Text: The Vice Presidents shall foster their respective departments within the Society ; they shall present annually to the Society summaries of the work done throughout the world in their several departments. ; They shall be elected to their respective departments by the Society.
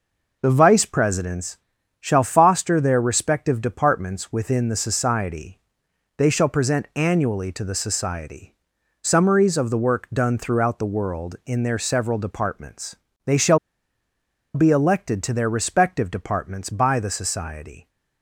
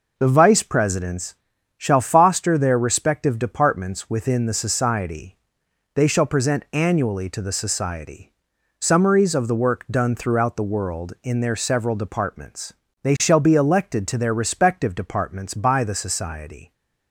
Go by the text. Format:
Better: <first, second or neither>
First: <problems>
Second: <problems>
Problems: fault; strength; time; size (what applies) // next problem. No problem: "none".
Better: second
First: pauses between "Presidents" and "shall"; at 1.5 s; 0.42 s long // pauses between "Society" and "summaries"; noticeable; at 8.5 s; 0.48 s long // pauses between "shall" and "be"; noticeable; at 13.5 s; 0.96 s long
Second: pauses between "Presidents" and "shall"; at 1.3 s; 0.42 s long // pauses between "Society" and "summaries"; noticeable; at 8.3 s; 0.48 s long